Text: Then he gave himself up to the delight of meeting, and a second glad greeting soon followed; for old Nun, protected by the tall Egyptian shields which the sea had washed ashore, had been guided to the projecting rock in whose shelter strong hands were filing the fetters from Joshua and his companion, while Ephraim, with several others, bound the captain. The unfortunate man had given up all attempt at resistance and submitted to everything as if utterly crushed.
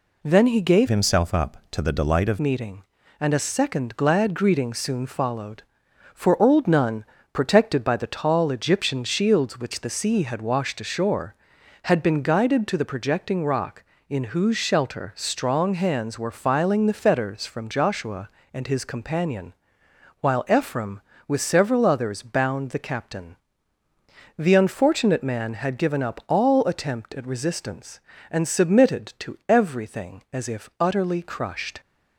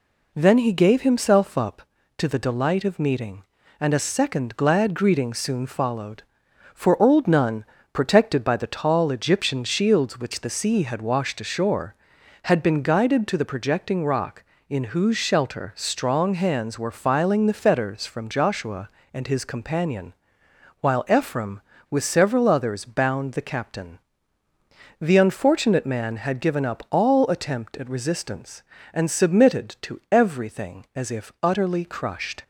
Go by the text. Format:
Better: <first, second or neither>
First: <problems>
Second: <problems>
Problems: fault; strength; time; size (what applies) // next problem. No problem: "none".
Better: second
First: changes voice from "himself" to "of"; from 0.8 to 2.3 s; 1.5 s long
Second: none